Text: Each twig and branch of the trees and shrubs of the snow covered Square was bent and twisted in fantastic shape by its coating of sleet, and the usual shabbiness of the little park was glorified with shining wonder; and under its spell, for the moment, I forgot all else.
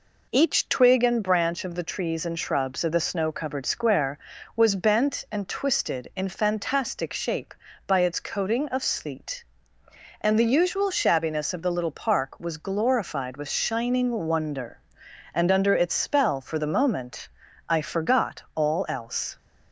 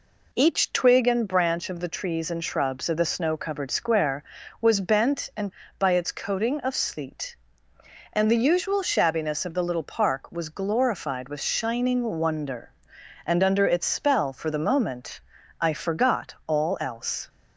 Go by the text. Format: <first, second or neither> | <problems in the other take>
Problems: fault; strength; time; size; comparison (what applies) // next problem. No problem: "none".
first | skips "twisted in fantastic shape"; at 5.6 s // pauses between "shining" and "wonder"; slight; at 12.0 s; 0.16 s long; slight in the first